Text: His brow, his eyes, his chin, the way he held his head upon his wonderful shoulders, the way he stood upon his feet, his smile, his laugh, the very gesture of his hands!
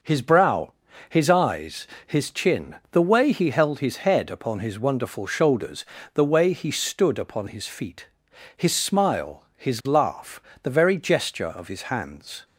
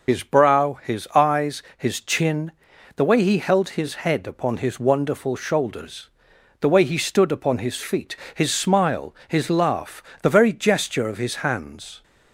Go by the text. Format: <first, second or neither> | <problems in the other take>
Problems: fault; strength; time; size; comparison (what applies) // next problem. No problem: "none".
first | loses the start of "His"; at 0.0 s; 80 ms